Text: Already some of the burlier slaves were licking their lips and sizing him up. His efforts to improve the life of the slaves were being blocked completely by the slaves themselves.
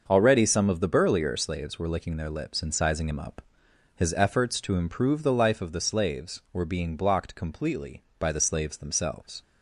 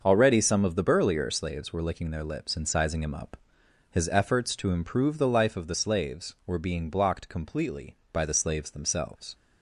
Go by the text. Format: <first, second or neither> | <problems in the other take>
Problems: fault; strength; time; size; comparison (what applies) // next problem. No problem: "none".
neither | starts louder than the rest; the same in both